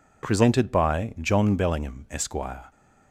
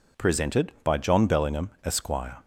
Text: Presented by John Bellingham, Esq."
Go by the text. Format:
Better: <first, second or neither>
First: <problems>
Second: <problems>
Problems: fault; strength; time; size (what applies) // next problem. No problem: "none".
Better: neither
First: none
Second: none